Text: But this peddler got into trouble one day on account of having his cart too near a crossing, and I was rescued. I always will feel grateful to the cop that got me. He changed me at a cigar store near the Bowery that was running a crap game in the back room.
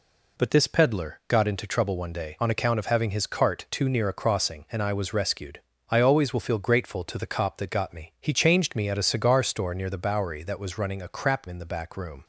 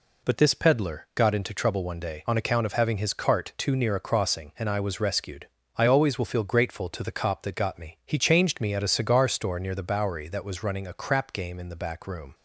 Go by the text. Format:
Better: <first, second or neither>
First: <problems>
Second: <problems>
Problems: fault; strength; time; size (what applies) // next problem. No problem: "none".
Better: second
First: skips "game"; at 11.4 s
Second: none